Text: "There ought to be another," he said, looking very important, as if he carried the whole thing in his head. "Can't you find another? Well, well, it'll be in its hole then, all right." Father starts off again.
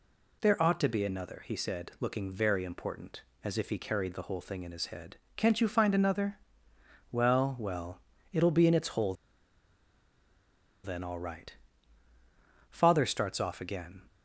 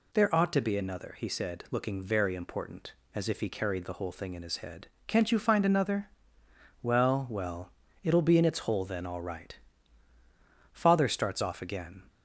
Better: second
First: pauses between "hole" and "then"; strong; at 9.1 s; 1.7 s long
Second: none

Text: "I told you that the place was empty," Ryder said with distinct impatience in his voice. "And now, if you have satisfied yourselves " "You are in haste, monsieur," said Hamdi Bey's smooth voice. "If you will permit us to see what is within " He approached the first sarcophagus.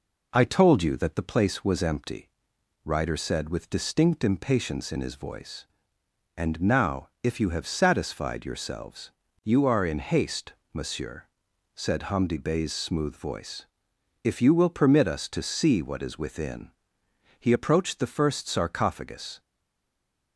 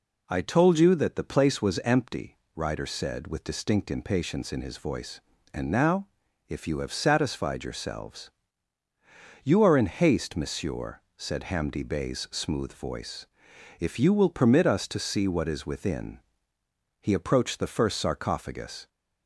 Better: second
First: stays silent after the last word; from 19.4 s on; 0.9 s long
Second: none

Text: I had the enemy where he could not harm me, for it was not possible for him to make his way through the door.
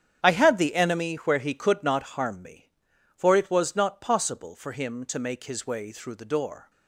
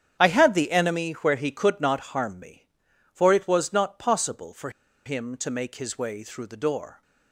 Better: first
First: starts louder than the rest; strong; until 1.2 s; 9 dB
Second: starts louder than the rest; strong; until 1.2 s; 9 dB // pauses between "for" and "him"; slight; at 4.6 s; 0.35 s long

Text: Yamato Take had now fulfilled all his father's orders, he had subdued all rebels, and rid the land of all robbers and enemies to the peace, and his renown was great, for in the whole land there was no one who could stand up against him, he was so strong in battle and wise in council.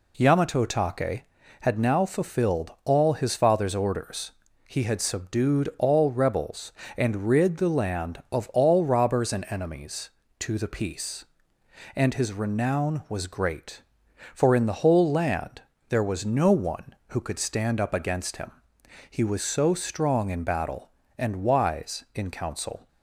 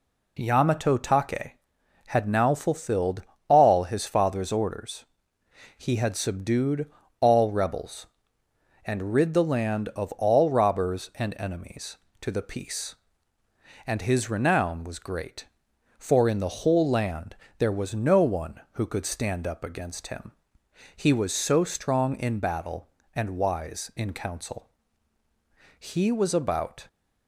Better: first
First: pauses between "land" and "there"; slight; at 15.6 s; 0.28 s long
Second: pauses between "fulfilled" and "all"; slight; at 3.2 s; 0.24 s long // pauses between "subdued" and "all"; slight; at 6.8 s; 0.32 s long // pauses between "land" and "there"; slight; at 17.3 s; 0.22 s long // goes on to say "He was about"; noticeable; from 25.7 s on; 1.0 s long

